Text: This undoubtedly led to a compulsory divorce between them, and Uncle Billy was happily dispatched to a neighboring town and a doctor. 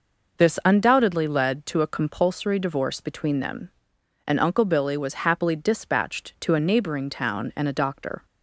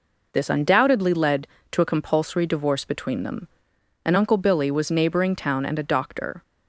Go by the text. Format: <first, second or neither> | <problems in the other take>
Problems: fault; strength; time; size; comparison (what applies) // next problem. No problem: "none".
first | skips "happily dispatched to a"; at 4.8 s